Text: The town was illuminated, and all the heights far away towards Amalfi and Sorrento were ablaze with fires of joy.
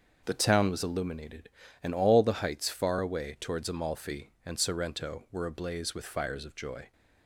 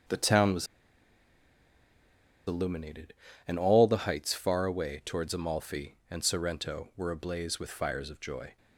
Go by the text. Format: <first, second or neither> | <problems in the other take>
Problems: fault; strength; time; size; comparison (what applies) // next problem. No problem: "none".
first | starts louder than the rest; until 2.9 s; 6.5 dB; also in the first // pauses between "was" and "illuminated"; strong; at 0.6 s; 1.8 s long